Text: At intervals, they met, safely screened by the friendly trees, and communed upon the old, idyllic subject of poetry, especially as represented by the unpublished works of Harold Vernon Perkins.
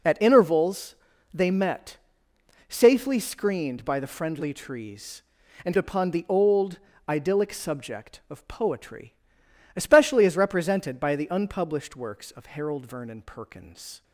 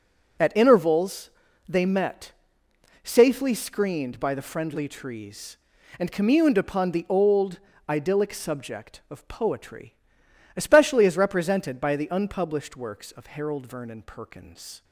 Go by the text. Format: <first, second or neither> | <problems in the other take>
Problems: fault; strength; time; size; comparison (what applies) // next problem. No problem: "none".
second | skips "communed"; at 5.7 s